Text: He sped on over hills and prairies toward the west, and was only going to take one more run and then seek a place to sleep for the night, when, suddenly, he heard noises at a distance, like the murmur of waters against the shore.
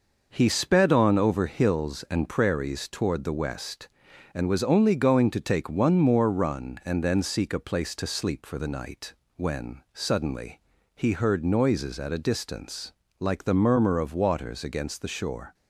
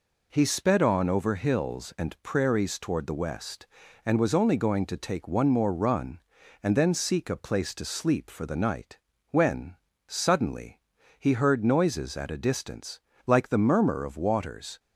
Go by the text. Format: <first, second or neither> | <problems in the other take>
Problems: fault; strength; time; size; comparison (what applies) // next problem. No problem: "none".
first | stops before "against the shore"; at 14.7 s